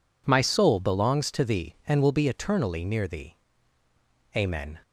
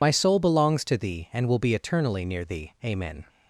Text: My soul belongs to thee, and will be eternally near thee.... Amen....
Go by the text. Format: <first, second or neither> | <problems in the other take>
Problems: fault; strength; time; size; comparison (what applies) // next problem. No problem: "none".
first | loses the start of "My"; at 0.0 s; 50 ms